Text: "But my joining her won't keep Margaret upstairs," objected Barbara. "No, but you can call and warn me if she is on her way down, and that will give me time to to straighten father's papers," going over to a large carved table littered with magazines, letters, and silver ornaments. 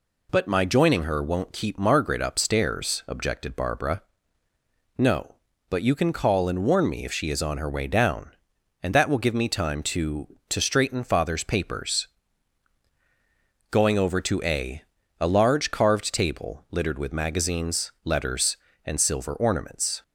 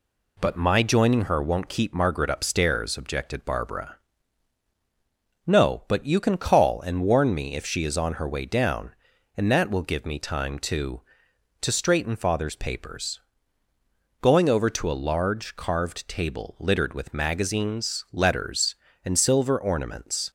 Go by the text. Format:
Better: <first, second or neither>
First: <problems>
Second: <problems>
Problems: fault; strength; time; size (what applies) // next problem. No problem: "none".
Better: second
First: says "a" twice; at 15.1 s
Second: none